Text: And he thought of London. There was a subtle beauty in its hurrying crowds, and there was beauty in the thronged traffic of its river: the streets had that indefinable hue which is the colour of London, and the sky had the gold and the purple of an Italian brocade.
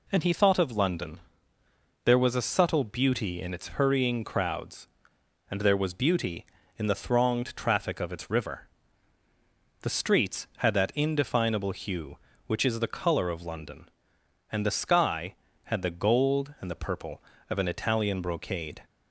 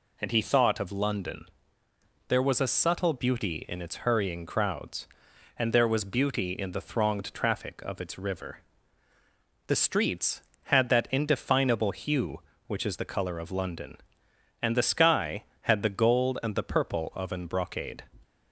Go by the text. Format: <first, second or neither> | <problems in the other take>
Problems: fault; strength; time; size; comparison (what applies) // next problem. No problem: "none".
first | skips "Italian"; at 17.4 s